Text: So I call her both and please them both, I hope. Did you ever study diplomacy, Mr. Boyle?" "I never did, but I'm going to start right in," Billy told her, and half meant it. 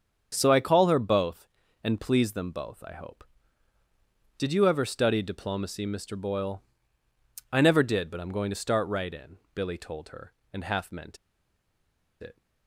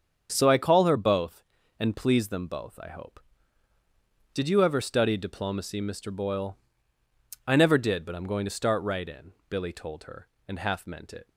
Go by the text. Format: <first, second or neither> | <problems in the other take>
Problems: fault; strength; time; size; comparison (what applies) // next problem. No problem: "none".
second | starts louder than the rest; strong; until 1.3 s; 7.5 dB; strong in the second // pauses between "meant" and "it"; at 11.1 s; 1.0 s long